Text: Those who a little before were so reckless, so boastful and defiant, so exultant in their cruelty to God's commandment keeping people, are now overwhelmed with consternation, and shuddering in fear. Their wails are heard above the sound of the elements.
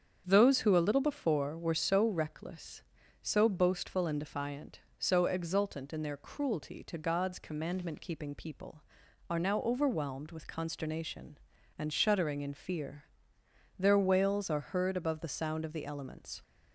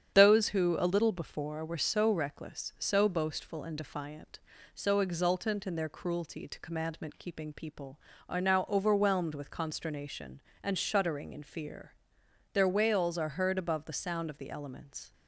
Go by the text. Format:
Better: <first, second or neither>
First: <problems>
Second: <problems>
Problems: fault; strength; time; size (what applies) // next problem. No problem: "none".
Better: first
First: starts louder than the rest; strong; until 1.2 s; 7.5 dB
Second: starts louder than the rest; strong; until 1.1 s; 8.5 dB // skips "God's"; at 6.5 s